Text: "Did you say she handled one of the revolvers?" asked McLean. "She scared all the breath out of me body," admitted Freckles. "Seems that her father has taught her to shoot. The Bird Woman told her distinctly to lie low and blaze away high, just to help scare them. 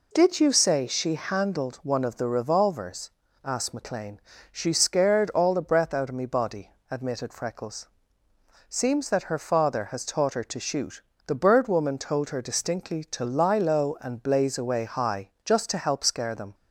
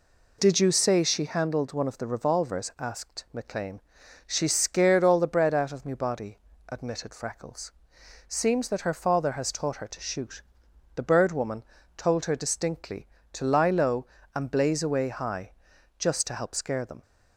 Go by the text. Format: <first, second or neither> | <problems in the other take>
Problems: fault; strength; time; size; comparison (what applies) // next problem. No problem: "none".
first | says "bread" for "breath"; at 5.2 s // pauses between "Woman" and "told"; slight; at 11.6 s; 0.32 s long